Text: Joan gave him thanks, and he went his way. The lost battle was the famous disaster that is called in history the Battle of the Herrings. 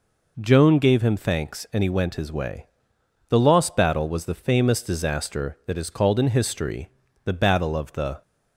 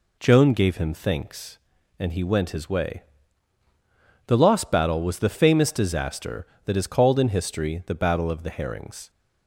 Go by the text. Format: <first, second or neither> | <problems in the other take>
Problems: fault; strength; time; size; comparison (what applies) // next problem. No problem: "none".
second | pauses between "history" and "the"; slight; at 6.8 s; 0.34 s long // stops before "Herrings"; at 8.2 s